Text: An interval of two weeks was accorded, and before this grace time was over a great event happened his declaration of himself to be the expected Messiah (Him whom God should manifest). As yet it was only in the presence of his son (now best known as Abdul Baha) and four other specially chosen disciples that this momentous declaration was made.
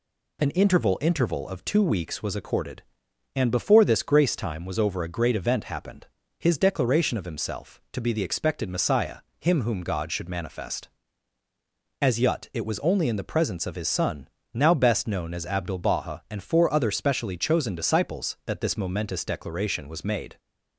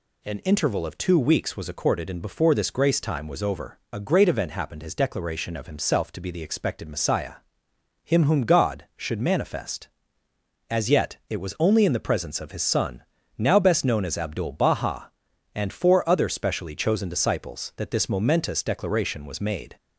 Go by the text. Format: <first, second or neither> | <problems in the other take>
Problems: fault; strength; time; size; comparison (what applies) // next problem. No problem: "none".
second | says "interval" twice; at 1.0 s // pauses between "happened" and "his"; slight; at 6.0 s; 0.32 s long